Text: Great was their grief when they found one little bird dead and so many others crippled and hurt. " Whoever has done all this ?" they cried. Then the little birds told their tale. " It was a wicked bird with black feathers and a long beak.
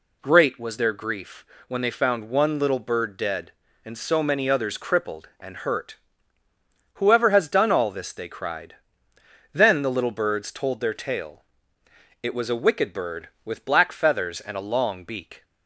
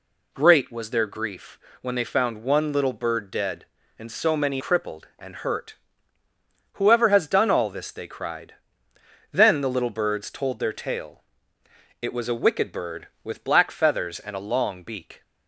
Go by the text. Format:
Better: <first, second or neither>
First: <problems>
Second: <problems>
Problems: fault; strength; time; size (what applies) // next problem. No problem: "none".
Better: first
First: pauses between "grief" and "when"; slight; at 1.4 s; 0.22 s long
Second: pauses between "grief" and "when"; slight; at 1.5 s; 0.22 s long // skips "others"; at 4.6 s